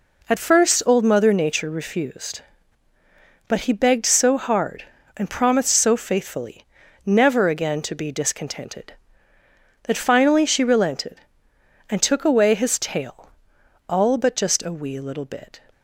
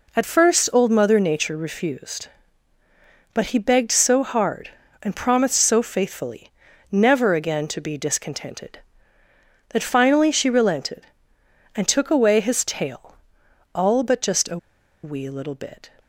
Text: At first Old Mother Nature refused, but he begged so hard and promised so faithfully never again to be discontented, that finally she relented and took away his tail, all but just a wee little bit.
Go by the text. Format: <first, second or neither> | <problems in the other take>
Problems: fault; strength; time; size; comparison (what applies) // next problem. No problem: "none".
first | pauses between "faithfully" and "never"; at 6.5 s; 0.40 s long; also in the first // pauses between "a" and "wee"; noticeable; at 14.5 s; 0.46 s long